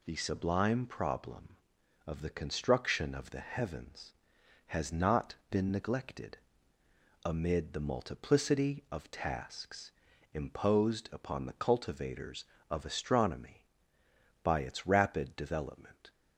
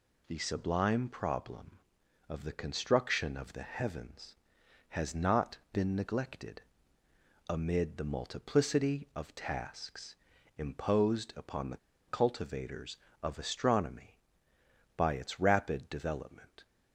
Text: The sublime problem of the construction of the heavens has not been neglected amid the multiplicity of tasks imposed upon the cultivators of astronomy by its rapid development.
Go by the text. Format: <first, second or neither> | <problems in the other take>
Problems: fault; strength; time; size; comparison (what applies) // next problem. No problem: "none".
first | pauses between "not" and "been"; slight; at 5.5 s; 0.16 s long; slight in the first // pauses between "neglected" and "amid"; noticeable; at 6.6 s; 0.84 s long; noticeable in the first // pauses between "tasks" and "imposed"; at 10.1 s; 0.40 s long; also in the first // pauses between "the" and "cultivators"; slight; at 11.7 s; 0.31 s long